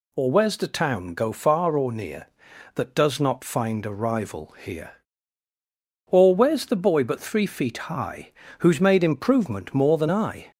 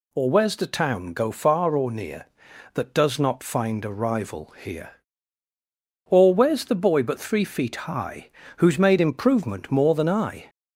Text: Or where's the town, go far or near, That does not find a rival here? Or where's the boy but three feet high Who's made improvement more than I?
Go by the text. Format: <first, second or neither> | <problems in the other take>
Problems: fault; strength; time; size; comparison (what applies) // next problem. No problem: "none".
neither | pauses between "high" and "Who's"; slight; the same in both